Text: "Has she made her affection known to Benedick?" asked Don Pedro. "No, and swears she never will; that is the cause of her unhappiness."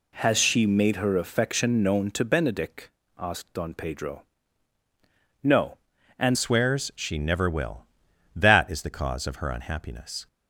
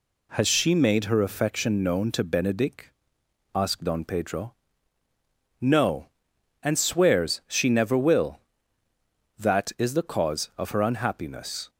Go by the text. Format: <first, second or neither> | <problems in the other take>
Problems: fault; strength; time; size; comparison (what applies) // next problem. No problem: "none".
second | changes voice at "swears"; from 6.3 s on; 3.9 s long